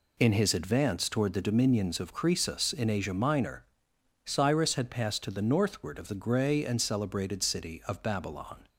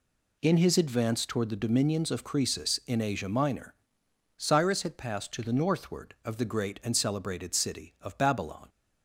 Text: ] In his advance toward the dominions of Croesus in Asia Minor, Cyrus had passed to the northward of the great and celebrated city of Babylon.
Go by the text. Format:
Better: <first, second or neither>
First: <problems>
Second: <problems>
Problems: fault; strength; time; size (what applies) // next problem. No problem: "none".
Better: second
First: says "grey" for "great"; at 6.1 s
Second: none